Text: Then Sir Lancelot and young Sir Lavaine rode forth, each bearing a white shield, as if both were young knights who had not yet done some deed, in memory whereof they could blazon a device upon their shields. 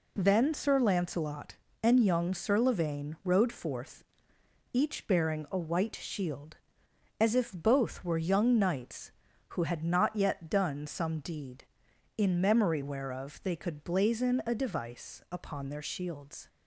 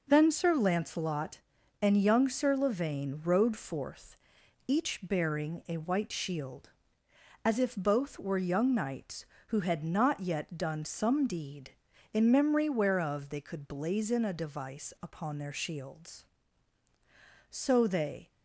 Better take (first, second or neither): first